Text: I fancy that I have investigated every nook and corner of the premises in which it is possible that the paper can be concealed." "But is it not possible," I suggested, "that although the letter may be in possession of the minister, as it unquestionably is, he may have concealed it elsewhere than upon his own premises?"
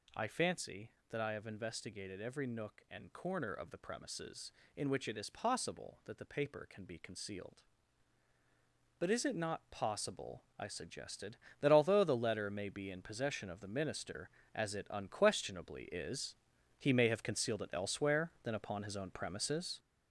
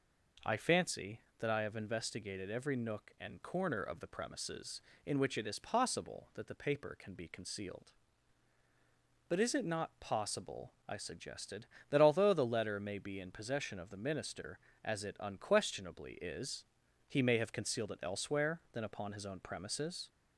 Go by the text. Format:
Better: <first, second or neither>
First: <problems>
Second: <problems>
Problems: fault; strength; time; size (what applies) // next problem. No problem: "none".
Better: second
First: gets louder; throughout; 6.5 dB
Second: none